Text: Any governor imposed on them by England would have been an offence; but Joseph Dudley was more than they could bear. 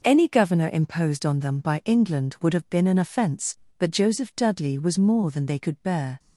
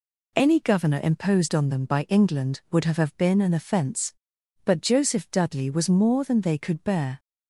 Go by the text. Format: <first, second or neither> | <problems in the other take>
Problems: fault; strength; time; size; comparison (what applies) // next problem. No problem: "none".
first | says "have" twice; at 2.9 s